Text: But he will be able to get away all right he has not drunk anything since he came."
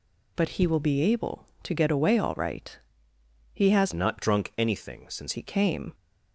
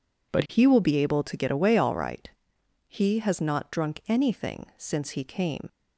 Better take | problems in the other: second | pauses between "right" and "he"; noticeable; at 2.7 s; 0.76 s long; noticeable in the second // changes voice from "not" to "since"; from 3.9 to 5.3 s; 1.4 s long

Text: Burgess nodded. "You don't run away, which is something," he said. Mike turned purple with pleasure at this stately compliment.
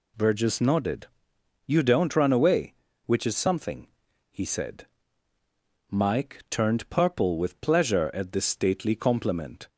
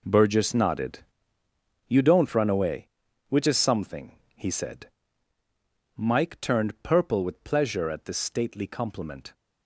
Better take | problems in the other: first | gets quieter; strong; throughout; 13 dB

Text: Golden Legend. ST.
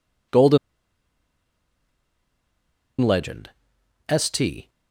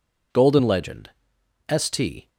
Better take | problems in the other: second | pauses between "Golden" and "Legend"; strong; at 0.5 s; 2.4 s long

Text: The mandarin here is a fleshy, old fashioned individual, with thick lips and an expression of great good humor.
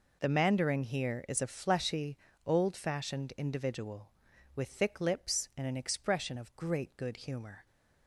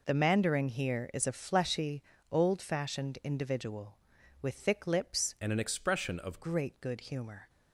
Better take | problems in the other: first | changes voice from "and" to "of"; from 5.3 to 6.4 s; 1.1 s long

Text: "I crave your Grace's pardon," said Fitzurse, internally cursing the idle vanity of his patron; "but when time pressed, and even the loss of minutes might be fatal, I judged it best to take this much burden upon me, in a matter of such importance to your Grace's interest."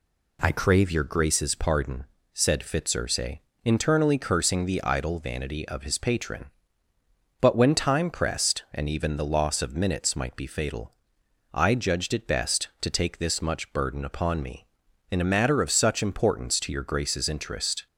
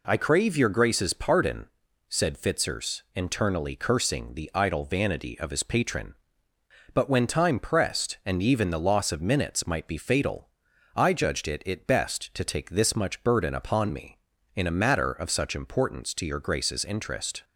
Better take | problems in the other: first | says "it" twice; at 11.6 s

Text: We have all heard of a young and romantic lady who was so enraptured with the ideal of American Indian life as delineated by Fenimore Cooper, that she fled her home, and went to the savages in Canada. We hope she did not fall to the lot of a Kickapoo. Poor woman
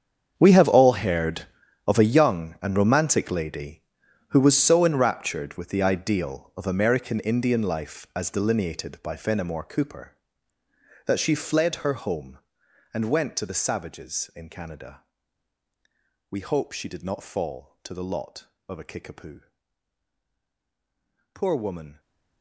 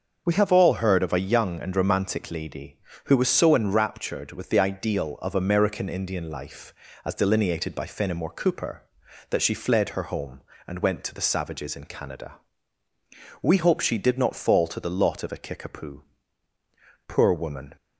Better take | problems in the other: second | gets quieter; strong; throughout; 16 dB // starts louder than the rest; strong; until 1.3 s; 7.5 dB; also in the second

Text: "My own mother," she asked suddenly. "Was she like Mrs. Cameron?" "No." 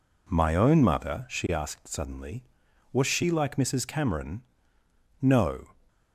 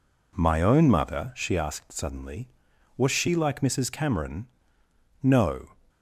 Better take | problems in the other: neither | none

